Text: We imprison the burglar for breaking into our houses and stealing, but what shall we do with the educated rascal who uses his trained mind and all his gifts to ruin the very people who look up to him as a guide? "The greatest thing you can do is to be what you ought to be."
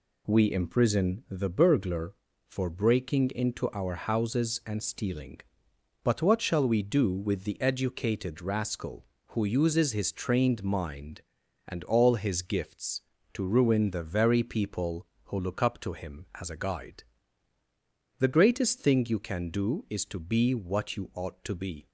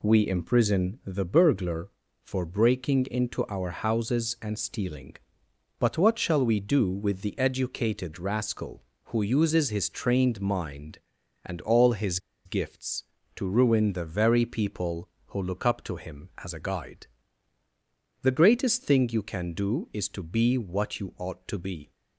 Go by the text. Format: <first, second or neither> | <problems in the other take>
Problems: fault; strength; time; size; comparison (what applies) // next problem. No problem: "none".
first | pauses between "his" and "gifts"; slight; at 12.1 s; 0.27 s long